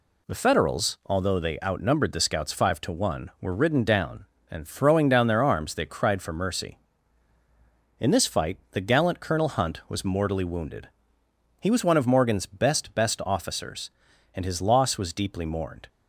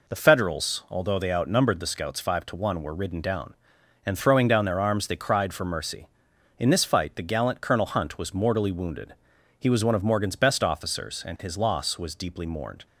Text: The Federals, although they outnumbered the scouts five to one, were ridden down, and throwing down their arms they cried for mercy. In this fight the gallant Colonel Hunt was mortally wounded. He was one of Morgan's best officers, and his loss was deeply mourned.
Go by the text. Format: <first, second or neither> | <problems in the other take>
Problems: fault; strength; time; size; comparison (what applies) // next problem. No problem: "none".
second | says "best" twice; at 12.9 s